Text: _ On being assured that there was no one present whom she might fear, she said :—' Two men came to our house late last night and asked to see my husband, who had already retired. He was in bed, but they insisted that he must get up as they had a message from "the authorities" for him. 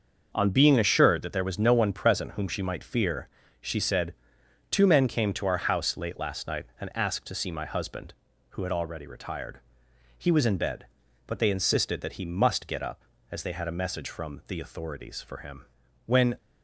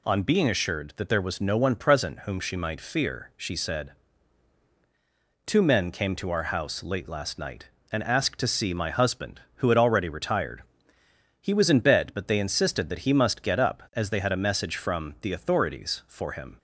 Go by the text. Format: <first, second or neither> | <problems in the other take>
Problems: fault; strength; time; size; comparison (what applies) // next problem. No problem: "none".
second | starts louder than the rest; until 1.3 s; 6.5 dB // goes on to say "When"; slight; from 16.0 s on; 0.32 s long